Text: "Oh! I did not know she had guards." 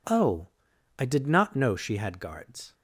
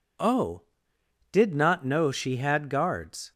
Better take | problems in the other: first | skips "I"; at 0.9 s

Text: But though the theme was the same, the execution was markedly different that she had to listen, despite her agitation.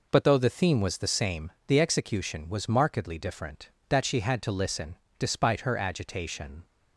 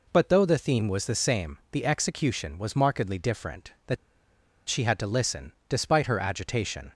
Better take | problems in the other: first | pauses between "that" and "she"; noticeable; at 3.9 s; 0.71 s long

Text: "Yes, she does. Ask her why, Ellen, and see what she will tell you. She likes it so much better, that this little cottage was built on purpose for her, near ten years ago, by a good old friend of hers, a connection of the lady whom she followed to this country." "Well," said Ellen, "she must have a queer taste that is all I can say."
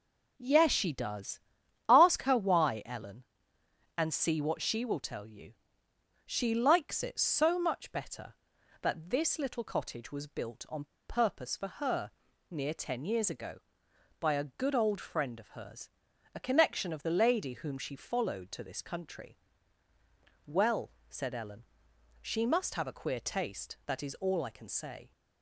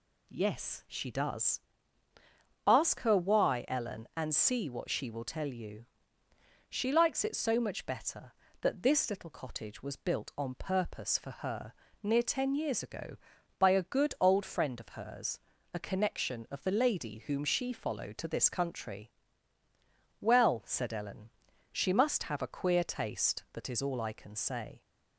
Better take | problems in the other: second | pauses between "on" and "purpose"; slight; at 10.8 s; 0.23 s long

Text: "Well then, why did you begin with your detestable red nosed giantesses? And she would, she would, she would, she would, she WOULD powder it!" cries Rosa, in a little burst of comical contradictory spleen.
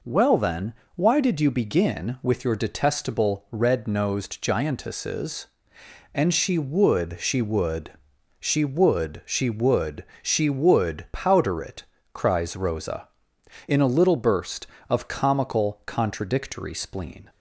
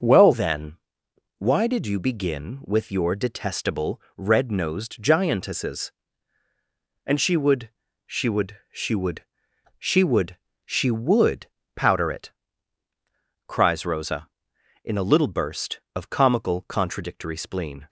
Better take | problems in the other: first | changes voice at "then"; from 0.3 s on; 17.5 s long // pauses between "detestable" and "red"; slight; at 4.0 s; 0.16 s long // pauses between "WOULD" and "powder"; slight; at 11.4 s; 0.30 s long

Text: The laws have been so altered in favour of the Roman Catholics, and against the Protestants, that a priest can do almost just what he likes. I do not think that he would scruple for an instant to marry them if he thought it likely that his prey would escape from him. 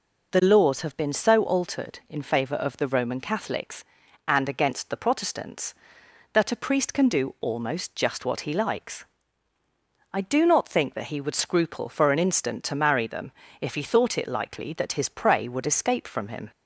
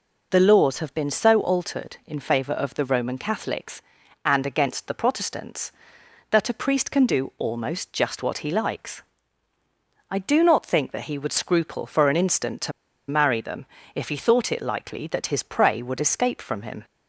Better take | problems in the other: first | pauses between "to" and "marry"; at 12.7 s; 0.38 s long // pauses between "them" and "if"; slight; at 13.6 s; 0.28 s long; slight in the first

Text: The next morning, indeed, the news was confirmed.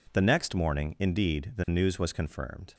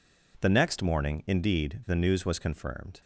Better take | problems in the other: neither | none

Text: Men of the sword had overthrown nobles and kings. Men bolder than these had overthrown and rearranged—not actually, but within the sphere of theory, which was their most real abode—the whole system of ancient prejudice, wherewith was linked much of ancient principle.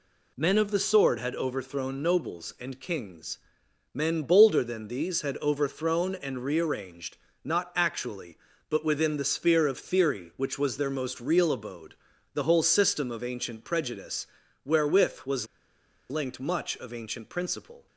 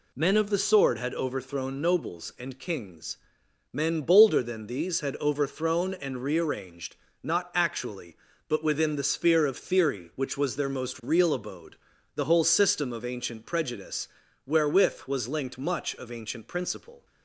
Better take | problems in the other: second | pauses between "was" and "linked"; noticeable; at 15.4 s; 0.64 s long

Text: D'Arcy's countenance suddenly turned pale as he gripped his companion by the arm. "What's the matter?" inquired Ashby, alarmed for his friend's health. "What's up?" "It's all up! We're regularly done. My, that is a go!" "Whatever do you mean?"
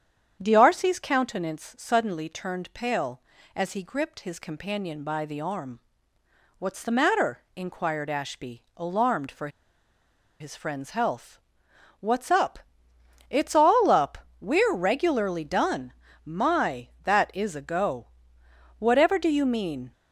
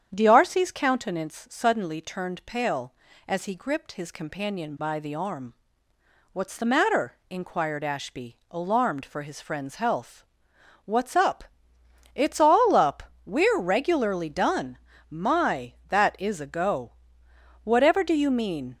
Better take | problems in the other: second | starts louder than the rest; strong; until 1.4 s; 8.5 dB; strong in the second // pauses between "for" and "his"; noticeable; at 9.4 s; 0.91 s long

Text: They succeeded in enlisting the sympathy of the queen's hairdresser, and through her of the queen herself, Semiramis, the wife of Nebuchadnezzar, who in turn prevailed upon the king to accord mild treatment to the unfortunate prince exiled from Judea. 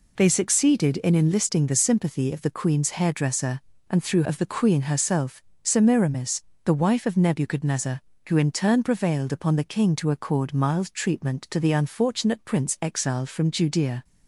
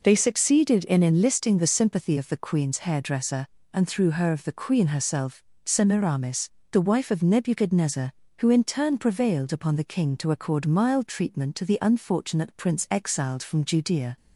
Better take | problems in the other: second | skips "her"; at 4.2 s

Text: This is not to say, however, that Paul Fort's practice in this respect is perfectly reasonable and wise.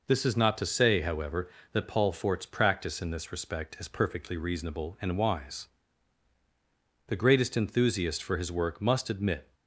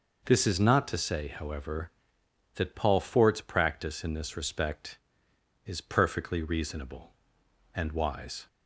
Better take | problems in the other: second | goes on to say "The greatest enthusiast for his work must admit"; strong; from 7.0 s on; 2.4 s long

